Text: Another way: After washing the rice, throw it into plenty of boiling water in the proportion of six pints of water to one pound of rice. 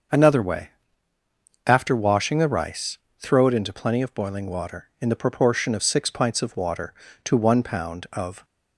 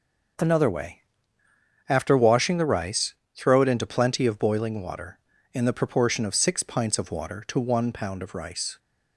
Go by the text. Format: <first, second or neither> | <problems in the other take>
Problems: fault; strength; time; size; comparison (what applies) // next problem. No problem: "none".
second | starts louder than the rest; until 2.0 s; 6.5 dB; also in the second // stops before "rice"; at 8.4 s